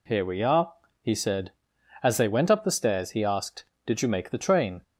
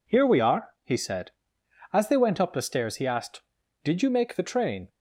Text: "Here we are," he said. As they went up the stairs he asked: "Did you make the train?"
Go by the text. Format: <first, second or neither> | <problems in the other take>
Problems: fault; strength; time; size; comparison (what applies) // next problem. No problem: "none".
neither | none